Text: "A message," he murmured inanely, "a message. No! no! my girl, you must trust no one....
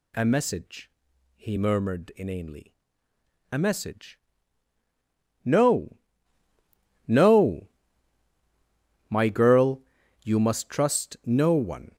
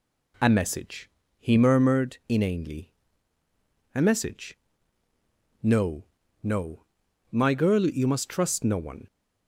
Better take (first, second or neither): neither